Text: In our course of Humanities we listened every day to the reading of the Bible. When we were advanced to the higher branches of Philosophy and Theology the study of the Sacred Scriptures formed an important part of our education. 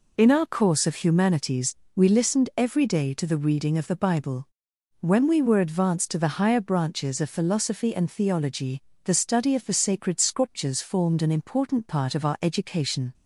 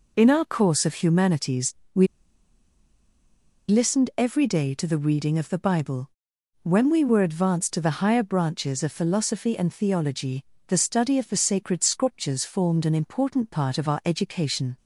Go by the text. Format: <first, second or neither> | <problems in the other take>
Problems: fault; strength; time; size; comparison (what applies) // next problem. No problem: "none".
first | pauses between "Humanities" and "we"; slight; at 1.7 s; 0.22 s long; slight in the first // pauses between "we" and "listened"; strong; at 2.0 s; 1.6 s long // pauses between "Theology" and "the"; slight; at 10.4 s; 0.22 s long; slight in the first